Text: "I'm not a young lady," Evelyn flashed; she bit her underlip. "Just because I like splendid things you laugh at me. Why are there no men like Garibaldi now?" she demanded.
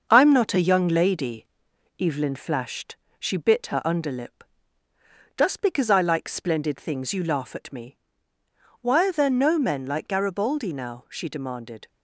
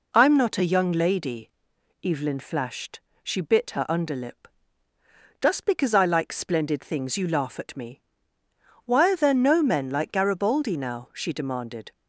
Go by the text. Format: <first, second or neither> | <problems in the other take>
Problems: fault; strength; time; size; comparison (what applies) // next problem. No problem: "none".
second | gets quieter; noticeable; throughout; 5 dB